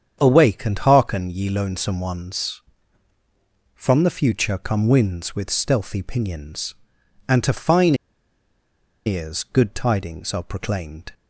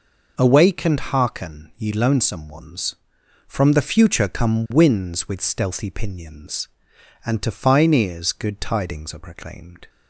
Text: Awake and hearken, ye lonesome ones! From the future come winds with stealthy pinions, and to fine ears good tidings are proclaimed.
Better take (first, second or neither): second